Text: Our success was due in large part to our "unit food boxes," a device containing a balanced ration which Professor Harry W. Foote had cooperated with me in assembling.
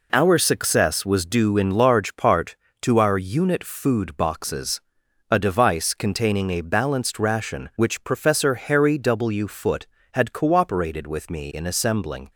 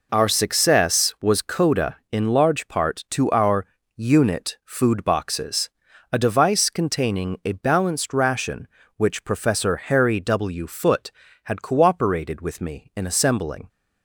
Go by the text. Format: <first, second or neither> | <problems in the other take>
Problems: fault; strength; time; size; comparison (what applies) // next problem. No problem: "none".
first | says "coda" for "due"; at 1.4 s // pauses between "our" and "unit"; slight; at 3.6 s; 0.28 s long